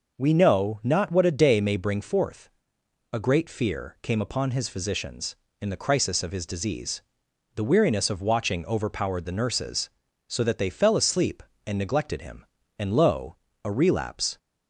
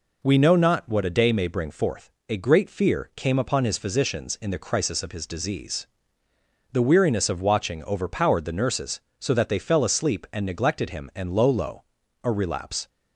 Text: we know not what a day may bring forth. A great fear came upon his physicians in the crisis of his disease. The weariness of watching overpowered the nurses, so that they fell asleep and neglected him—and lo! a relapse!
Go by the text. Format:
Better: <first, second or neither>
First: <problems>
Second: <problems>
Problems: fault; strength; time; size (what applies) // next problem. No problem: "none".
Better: first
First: none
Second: says "lo" twice; at 11.4 s